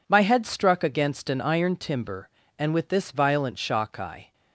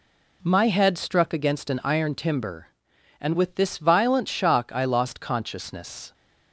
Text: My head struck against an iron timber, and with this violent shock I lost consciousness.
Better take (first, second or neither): second